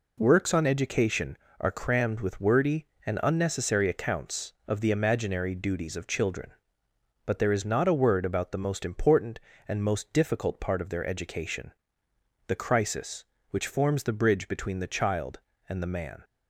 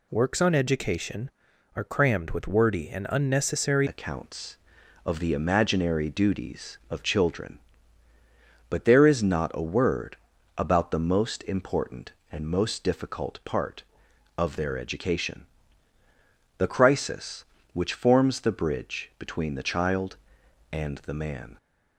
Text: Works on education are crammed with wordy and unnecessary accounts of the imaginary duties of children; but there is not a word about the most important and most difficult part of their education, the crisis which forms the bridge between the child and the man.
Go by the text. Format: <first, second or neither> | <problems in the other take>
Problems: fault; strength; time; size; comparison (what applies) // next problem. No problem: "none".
first | changes voice at "accounts"; from 3.8 s on; 17.7 s long // pauses between "word" and "about"; at 10.1 s; 0.40 s long